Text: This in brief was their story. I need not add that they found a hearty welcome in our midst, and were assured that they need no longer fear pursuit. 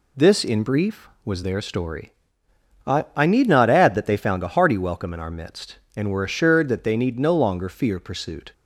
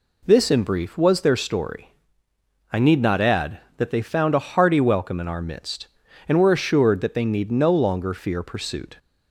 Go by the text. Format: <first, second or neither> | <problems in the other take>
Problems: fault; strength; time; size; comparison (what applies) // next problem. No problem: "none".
second | says "I" twice; at 3.1 s